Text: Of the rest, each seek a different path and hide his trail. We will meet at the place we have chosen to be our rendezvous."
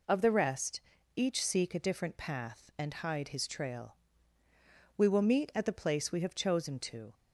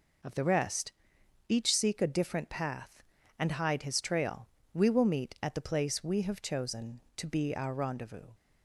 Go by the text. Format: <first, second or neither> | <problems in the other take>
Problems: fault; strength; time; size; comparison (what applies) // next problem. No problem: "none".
second | stops before "be our rendezvous"; at 7.1 s